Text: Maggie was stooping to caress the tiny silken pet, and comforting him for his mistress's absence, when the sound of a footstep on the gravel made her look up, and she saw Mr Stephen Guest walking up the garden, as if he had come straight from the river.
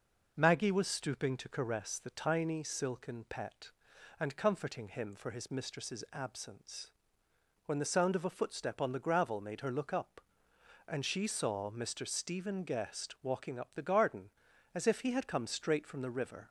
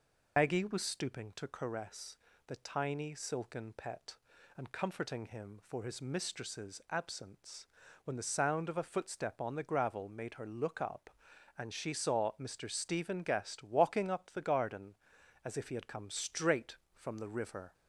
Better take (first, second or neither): first